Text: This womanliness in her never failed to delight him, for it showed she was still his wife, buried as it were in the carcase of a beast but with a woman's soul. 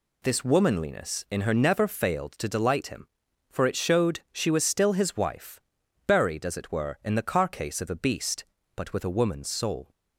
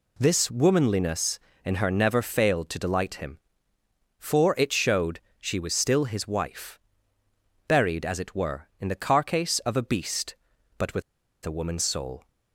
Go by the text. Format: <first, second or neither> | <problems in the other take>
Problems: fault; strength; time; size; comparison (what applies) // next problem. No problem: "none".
first | pauses between "showed" and "she"; slight; at 5.1 s; 0.20 s long // pauses between "with" and "a"; at 11.0 s; 0.43 s long